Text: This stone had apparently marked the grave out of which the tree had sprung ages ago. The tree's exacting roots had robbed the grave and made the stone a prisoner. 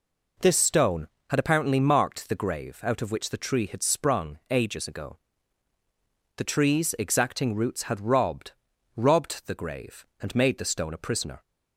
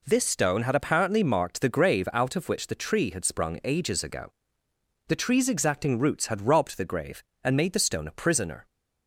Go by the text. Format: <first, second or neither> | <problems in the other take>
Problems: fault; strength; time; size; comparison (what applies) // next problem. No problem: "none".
second | says "robbed" twice; at 8.9 s